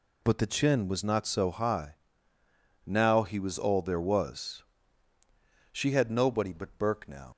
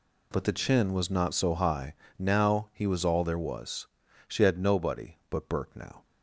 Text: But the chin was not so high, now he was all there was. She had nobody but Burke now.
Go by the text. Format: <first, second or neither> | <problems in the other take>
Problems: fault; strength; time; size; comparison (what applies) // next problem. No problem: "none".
second | leaves "now" unfinished; at 7.3 s; 100 ms